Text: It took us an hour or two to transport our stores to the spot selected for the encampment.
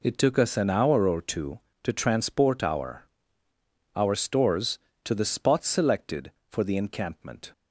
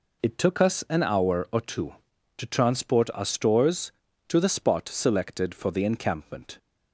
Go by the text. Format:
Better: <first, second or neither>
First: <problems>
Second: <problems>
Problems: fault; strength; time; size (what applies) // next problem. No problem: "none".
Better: second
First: says "our" twice; at 3.9 s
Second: none